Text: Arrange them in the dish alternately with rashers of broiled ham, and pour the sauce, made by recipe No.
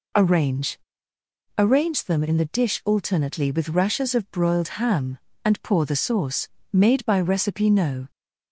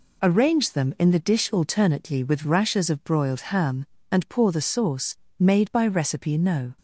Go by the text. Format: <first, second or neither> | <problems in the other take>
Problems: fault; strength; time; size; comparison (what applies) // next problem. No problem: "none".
second | says "Arrange" twice; at 1.5 s